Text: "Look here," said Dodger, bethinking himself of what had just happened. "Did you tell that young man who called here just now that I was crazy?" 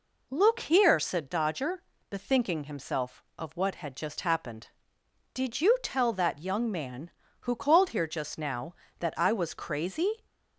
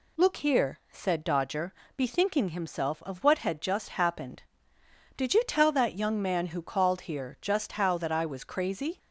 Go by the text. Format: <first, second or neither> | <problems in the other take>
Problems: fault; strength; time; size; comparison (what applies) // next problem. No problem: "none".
first | says "how" for "now"; at 7.7 s